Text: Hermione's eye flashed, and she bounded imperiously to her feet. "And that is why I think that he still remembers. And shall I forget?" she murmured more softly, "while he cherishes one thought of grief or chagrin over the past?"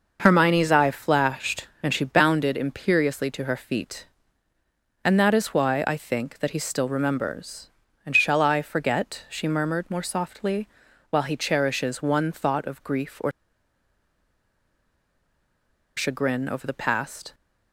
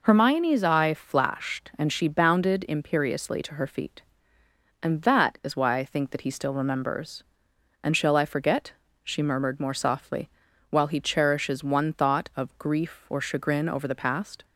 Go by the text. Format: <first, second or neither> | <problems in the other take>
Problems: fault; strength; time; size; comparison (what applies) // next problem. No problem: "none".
second | pauses between "or" and "chagrin"; strong; at 13.3 s; 2.6 s long